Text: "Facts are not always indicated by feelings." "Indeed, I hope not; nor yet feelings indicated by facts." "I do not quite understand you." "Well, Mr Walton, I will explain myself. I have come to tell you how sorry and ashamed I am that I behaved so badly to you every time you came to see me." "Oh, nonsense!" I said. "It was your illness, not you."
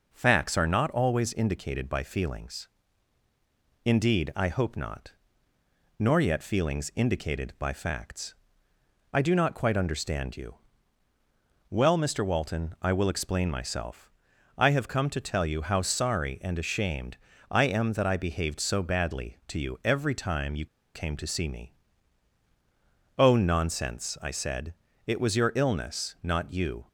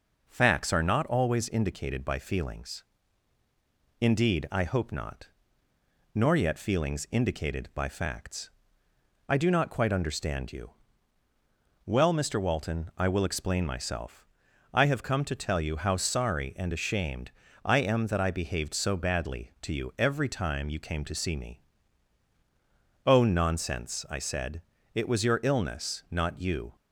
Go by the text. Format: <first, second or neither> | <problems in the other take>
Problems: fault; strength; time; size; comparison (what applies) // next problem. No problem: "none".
second | pauses between "ashamed" and "I"; slight; at 17.1 s; 0.32 s long; slight in the second // pauses between "you" and "came"; slight; at 20.6 s; 0.29 s long